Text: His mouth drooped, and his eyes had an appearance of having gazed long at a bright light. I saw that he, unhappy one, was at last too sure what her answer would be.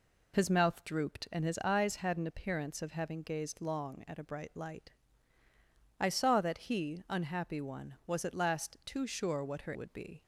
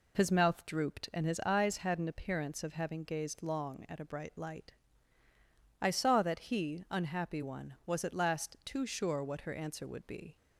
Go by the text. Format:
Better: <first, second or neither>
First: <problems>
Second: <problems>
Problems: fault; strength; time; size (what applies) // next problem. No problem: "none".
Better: second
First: skips "answer"; at 9.7 s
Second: none